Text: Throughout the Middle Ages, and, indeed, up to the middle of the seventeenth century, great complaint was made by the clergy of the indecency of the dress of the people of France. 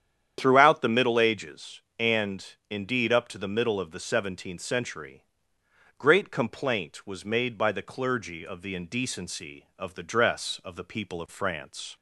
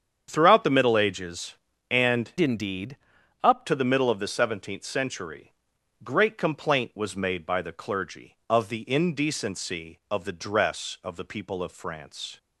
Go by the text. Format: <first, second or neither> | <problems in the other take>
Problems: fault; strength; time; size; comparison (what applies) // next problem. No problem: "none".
first | starts louder than the rest; strong; until 1.3 s; 8 dB; strong in the first // changes voice from "indeed" to "up"; from 2.3 to 3.6 s; 1.3 s long